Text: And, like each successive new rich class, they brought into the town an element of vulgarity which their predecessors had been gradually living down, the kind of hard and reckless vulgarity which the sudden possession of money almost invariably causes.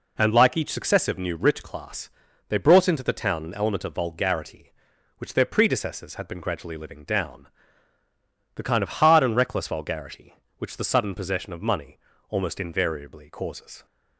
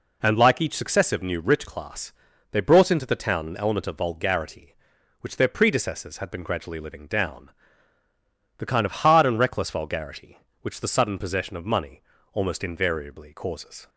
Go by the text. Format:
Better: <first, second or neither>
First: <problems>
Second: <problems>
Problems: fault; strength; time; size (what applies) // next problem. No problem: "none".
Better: neither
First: pauses between "money" and "almost"; slight; at 11.9 s; 0.32 s long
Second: pauses between "money" and "almost"; slight; at 12.0 s; 0.32 s long